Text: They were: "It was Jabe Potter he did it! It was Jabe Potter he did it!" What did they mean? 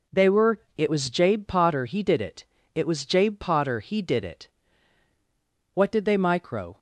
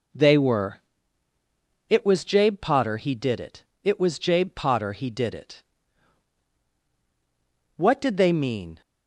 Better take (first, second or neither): second